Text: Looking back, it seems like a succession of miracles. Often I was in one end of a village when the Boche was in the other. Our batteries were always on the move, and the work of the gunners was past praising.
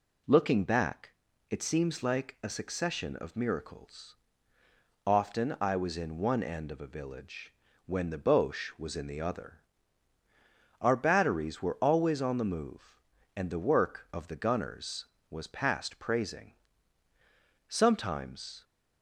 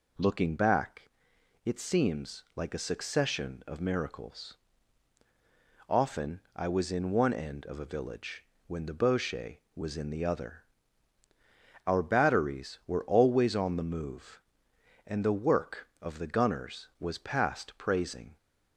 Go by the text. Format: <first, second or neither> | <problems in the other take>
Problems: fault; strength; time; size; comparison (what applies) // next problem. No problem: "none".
second | pauses between "village" and "when"; slight; at 7.5 s; 0.34 s long; slight in the second // goes on to say "Sometimes"; noticeable; from 17.6 s on; 0.96 s long